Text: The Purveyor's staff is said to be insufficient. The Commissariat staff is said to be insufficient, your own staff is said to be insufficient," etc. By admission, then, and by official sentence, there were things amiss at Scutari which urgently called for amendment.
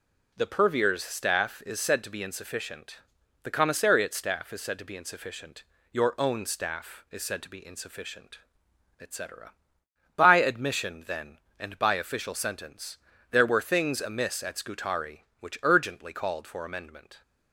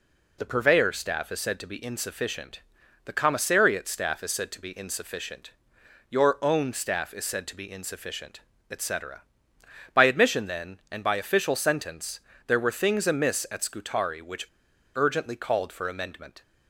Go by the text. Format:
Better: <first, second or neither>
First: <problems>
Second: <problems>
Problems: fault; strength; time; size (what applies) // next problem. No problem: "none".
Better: first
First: none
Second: pauses between "which" and "urgently"; noticeable; at 14.4 s; 0.46 s long